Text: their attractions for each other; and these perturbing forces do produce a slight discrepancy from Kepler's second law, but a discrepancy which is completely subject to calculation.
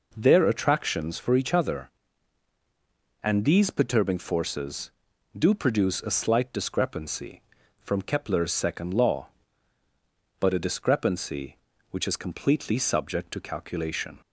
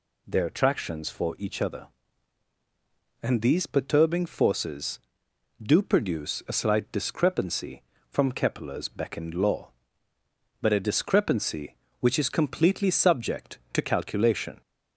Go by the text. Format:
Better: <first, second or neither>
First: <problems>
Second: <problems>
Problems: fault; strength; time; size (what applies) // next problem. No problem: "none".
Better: first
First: none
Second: says "beckoned" for "second"; at 8.8 s